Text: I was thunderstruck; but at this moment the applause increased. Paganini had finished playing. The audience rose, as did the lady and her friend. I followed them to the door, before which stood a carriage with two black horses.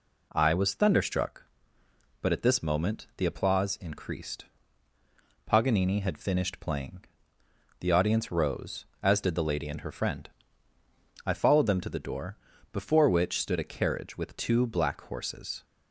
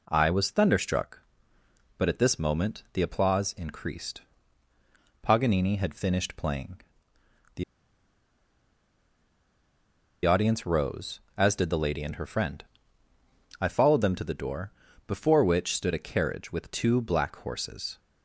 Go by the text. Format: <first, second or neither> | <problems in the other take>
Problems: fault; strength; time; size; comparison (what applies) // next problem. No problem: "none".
first | pauses between "The" and "audience"; strong; at 7.6 s; 2.6 s long